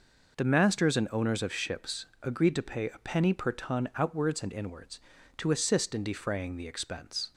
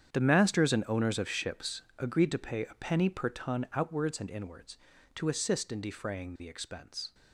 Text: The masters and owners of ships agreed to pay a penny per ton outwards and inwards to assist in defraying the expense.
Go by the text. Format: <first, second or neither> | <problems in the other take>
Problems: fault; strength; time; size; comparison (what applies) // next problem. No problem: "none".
first | gets quieter; strong; throughout; 15 dB // pauses between "ships" and "agreed"; slight; at 1.8 s; 0.16 s long; slight in the first